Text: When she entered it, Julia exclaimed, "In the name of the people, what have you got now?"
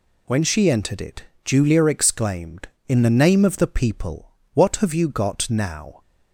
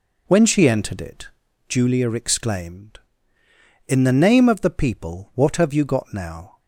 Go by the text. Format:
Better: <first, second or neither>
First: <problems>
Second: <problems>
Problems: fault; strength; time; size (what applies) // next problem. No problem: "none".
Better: first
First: none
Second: starts louder than the rest; noticeable; until 1.7 s; 4.5 dB